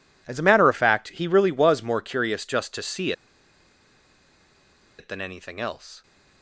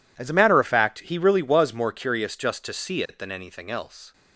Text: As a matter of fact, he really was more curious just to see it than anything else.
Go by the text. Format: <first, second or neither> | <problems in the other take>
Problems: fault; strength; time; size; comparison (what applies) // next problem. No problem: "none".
second | pauses between "see" and "it"; strong; at 3.1 s; 1.8 s long